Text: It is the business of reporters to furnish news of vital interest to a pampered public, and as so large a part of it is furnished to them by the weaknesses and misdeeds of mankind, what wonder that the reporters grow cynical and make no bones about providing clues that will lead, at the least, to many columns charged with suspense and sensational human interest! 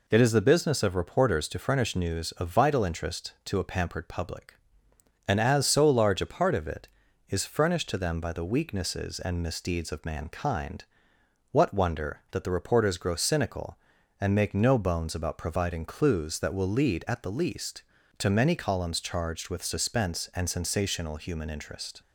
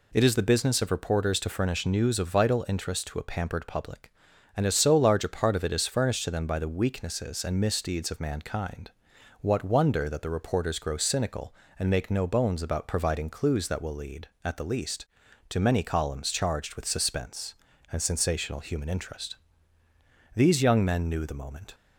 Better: first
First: none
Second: goes on to say "These young men knew the moment"; from 20.3 s on; 1.3 s long

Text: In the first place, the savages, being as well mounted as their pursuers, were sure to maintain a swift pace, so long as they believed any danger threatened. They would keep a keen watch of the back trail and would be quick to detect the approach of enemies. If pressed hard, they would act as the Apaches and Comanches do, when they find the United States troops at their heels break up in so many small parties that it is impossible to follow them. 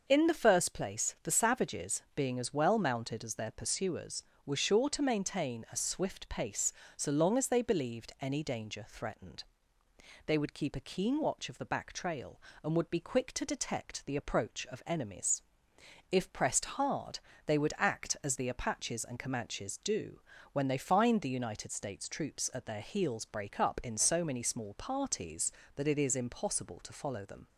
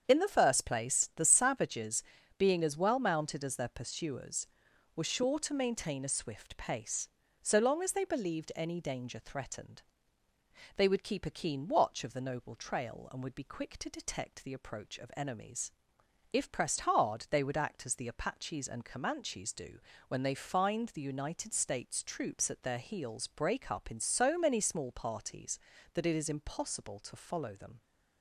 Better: first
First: starts louder than the rest; until 1.0 s; 6 dB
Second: starts louder than the rest; strong; until 1.0 s; 7.5 dB // says "noble" for "back"; at 12.2 s

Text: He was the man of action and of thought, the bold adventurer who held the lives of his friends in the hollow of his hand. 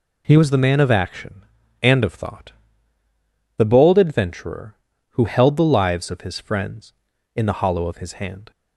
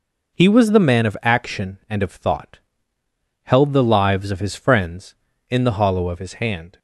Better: first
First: none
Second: skips "the bold adventurer who"; at 2.9 s

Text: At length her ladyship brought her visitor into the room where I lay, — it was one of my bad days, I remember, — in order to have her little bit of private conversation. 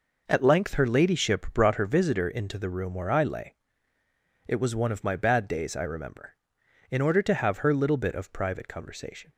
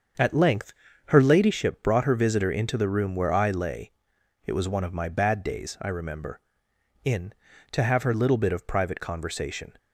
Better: first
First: none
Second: starts louder than the rest; until 1.5 s; 7 dB // pauses between "length" and "her"; slight; at 0.7 s; 0.36 s long // skips "order"; at 7.5 s

